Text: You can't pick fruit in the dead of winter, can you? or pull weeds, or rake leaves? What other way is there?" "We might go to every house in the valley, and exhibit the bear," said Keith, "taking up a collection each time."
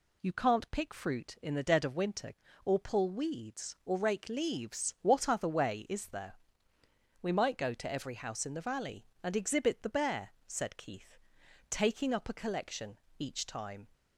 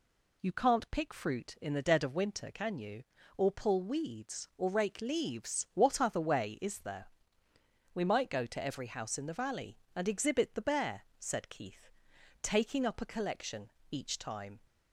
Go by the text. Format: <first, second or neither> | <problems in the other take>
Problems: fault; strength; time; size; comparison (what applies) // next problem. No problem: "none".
second | skips "can you"; at 2.4 s // pauses between "collection" and "each"; slight; at 12.9 s; 0.20 s long; slight in the second